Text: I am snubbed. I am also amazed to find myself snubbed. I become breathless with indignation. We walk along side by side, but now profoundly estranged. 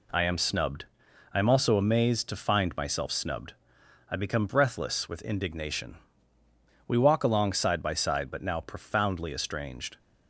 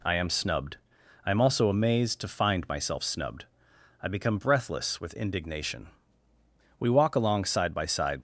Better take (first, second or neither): first